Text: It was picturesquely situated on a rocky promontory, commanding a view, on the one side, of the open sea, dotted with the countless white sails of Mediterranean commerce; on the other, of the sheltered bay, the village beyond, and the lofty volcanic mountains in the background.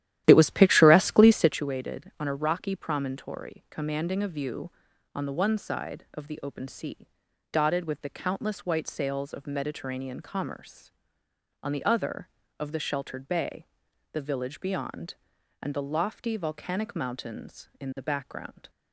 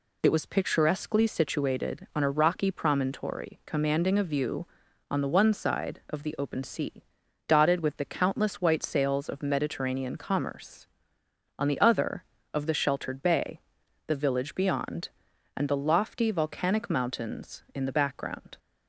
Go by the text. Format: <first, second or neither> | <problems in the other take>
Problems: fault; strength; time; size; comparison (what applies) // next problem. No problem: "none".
second | starts louder than the rest; strong; until 1.7 s; 13 dB